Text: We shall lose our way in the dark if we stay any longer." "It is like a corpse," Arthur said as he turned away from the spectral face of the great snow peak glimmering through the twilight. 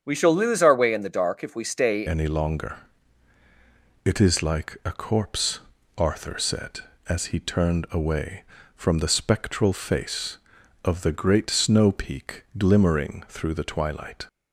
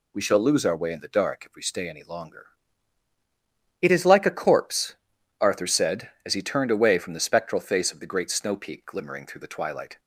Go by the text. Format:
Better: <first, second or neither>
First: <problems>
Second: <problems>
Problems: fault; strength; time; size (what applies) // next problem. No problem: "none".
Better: second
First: starts louder than the rest; strong; until 1.0 s; 7.5 dB // changes voice at "any"; from 2.0 s on; 12.2 s long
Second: none